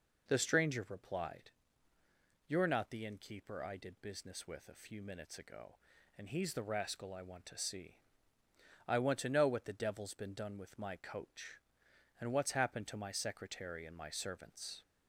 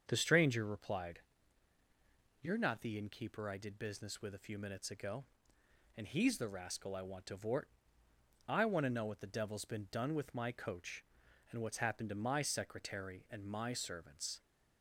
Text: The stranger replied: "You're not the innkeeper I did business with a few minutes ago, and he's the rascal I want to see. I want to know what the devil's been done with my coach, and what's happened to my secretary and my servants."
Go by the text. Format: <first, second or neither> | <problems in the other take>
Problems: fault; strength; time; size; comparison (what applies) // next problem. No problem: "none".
first | starts louder than the rest; until 1.0 s; 7 dB // says "vort" for "see"; at 7.3 s